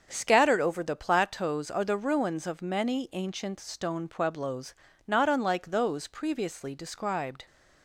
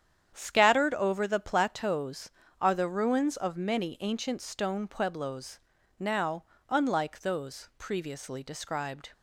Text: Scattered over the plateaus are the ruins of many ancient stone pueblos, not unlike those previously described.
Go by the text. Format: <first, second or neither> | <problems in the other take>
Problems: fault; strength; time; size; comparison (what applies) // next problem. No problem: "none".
first | starts louder than the rest; strong; until 1.3 s; 9 dB; also in the first // says "now" for "not"; at 5.9 s